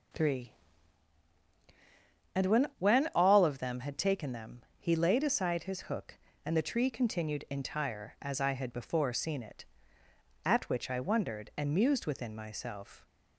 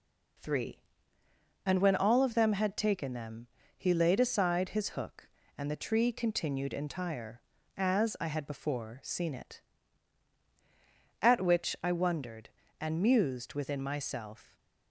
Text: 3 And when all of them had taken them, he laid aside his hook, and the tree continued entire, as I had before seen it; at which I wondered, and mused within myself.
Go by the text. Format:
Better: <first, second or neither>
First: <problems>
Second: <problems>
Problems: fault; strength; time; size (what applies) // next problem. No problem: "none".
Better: second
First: says "when" twice; at 2.7 s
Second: none